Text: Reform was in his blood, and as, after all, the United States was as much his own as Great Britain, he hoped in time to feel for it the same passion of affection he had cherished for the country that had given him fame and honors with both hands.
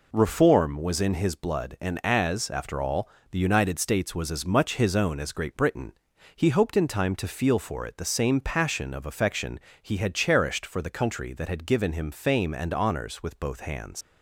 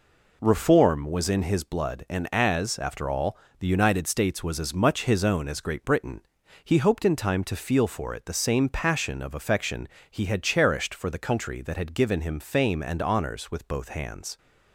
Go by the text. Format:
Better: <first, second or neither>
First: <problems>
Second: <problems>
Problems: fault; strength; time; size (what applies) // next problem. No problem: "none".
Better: second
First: pauses between "affection" and "he"; slight; at 9.5 s; 0.22 s long // leaves "hands" unfinished; at 14.0 s; 80 ms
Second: pauses between "affection" and "he"; slight; at 9.8 s; 0.22 s long